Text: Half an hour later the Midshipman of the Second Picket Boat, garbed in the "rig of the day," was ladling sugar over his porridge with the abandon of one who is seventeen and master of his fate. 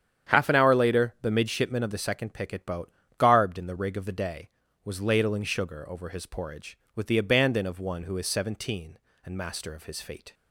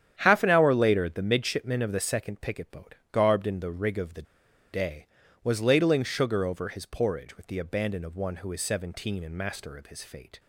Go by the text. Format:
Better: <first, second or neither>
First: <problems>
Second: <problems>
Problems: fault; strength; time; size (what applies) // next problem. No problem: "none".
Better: first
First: starts louder than the rest; strong; until 1.3 s; 9 dB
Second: starts louder than the rest; strong; until 1.1 s; 9.5 dB // pauses between "the" and "day"; noticeable; at 4.2 s; 0.50 s long